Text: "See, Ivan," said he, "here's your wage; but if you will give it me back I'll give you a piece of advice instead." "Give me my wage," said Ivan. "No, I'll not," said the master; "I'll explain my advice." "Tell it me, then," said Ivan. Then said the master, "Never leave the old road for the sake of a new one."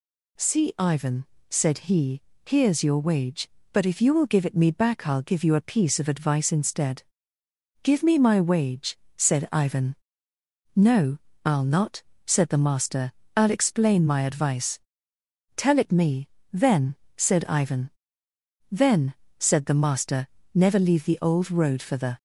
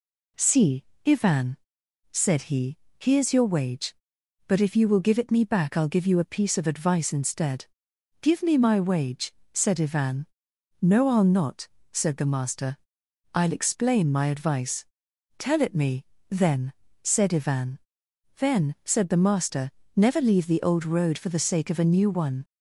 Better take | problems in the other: second | pauses between "Then" and "said"; slight; at 19.1 s; 0.26 s long // stops before "sake of a new one"; at 22.1 s

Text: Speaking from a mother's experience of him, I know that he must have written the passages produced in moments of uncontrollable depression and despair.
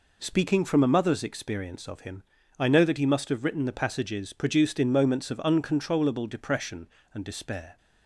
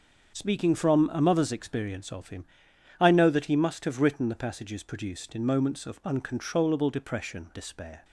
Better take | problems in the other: first | starts louder than the rest; until 1.3 s; 6.5 dB // skips "and"; at 7.5 s

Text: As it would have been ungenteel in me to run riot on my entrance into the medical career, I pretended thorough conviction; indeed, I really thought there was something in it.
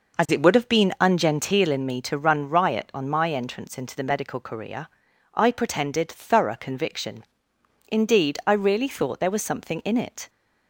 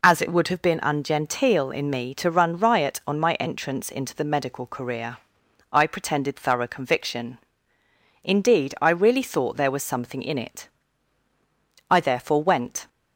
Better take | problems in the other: first | goes on to say "I therefore went"; noticeable; from 11.8 s on; 0.98 s long

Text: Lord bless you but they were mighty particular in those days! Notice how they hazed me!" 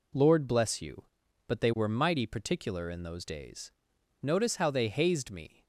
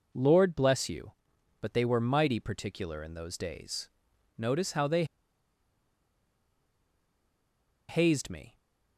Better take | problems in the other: first | pauses between "they" and "hazed"; strong; at 5.0 s; 2.8 s long

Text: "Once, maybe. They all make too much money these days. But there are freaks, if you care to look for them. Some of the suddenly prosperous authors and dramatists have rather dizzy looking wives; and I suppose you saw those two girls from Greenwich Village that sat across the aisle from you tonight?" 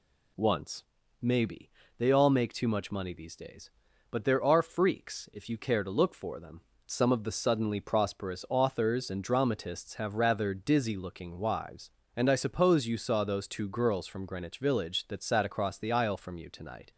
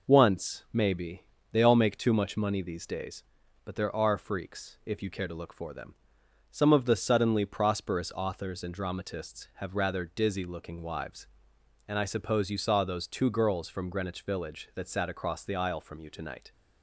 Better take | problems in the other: neither | none

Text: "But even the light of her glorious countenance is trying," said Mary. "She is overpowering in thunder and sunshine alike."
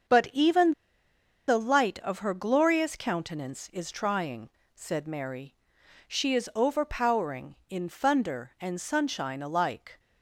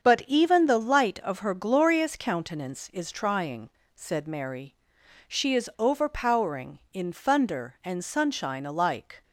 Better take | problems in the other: second | starts louder than the rest; strong; until 1.8 s; 7 dB; strong in the second // pauses between "even" and "the"; noticeable; at 0.7 s; 0.76 s long

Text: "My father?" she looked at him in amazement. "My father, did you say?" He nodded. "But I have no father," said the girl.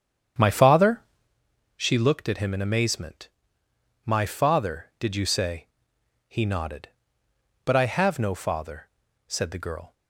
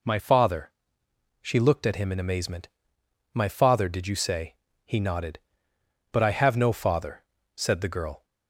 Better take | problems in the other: second | starts louder than the rest; strong; until 1.4 s; 8 dB

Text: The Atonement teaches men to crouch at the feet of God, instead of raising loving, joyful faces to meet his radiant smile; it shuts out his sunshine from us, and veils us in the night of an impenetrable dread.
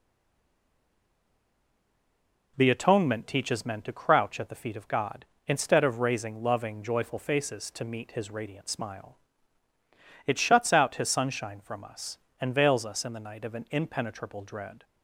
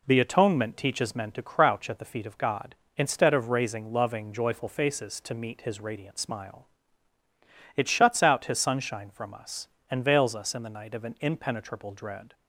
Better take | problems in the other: second | stays silent before the first word; strong; until 2.5 s; 2.5 s long

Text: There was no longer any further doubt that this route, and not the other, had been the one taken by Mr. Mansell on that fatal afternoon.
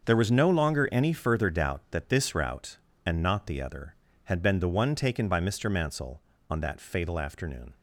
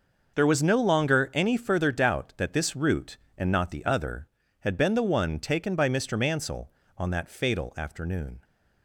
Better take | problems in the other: neither | starts louder than the rest; the same in both

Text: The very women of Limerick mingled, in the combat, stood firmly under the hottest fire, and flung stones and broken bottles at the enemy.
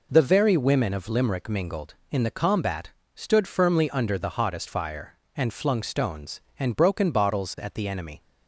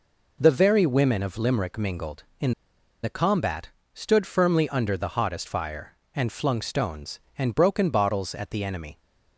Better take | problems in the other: first | pauses between "in" and "the"; noticeable; at 2.5 s; 0.51 s long

